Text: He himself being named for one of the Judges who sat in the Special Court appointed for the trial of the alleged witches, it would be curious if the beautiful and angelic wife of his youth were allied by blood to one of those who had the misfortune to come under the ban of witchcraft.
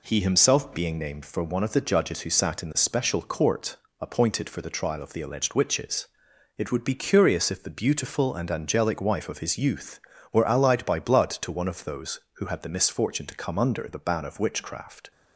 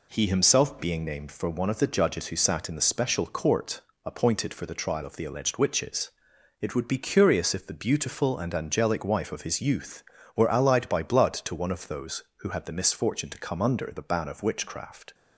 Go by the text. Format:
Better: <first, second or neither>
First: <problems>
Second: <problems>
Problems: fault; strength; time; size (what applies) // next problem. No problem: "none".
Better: neither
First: pauses between "Court" and "appointed"; slight; at 3.7 s; 0.24 s long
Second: pauses between "Court" and "appointed"; slight; at 3.8 s; 0.24 s long